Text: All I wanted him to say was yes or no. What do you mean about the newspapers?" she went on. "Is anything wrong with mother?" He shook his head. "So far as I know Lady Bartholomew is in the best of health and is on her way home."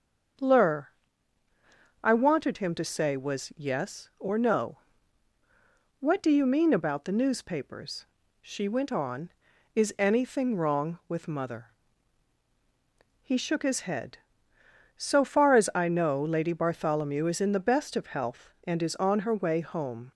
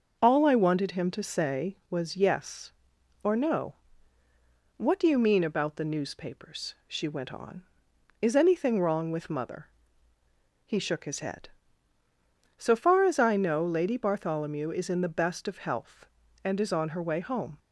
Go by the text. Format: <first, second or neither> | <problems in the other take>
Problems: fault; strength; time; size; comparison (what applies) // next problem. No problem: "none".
second | starts louder than the rest; until 2.5 s; 7 dB; noticeable in the second // says "Lur" for "All"; at 0.4 s